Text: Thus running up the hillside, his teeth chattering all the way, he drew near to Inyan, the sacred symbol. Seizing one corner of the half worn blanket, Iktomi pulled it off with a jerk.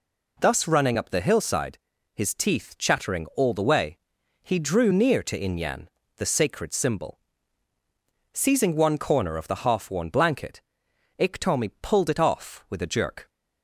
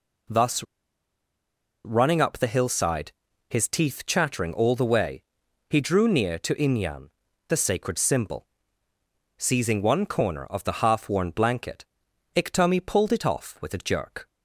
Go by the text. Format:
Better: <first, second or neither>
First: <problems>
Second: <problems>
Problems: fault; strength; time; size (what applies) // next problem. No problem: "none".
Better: first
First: none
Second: pauses between "Thus" and "running"; at 0.6 s; 1.2 s long